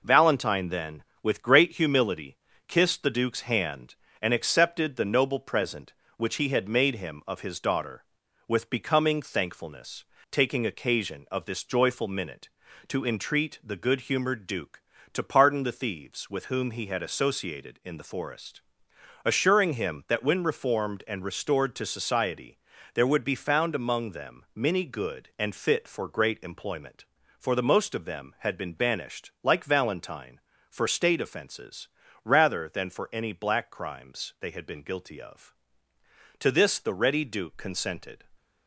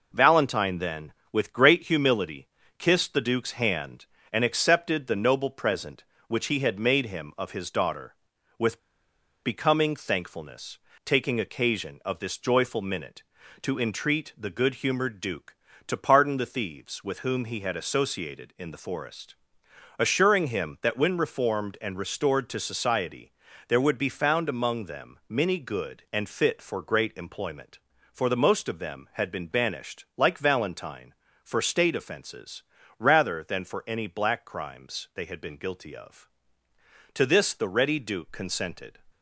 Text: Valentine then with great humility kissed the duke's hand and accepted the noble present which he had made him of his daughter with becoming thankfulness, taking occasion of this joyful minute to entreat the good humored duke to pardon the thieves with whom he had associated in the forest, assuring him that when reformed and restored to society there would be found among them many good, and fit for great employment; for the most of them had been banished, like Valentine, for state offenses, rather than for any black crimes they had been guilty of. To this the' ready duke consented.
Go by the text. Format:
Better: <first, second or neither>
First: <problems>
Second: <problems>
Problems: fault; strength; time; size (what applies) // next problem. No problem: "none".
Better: first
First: pauses between "humility" and "kissed"; slight; at 2.3 s; 0.30 s long // pauses between "society" and "there"; slight; at 22.5 s; 0.36 s long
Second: pauses between "humility" and "kissed"; slight; at 2.4 s; 0.30 s long // pauses between "with" and "becoming"; noticeable; at 8.7 s; 0.64 s long // pauses between "society" and "there"; slight; at 23.3 s; 0.36 s long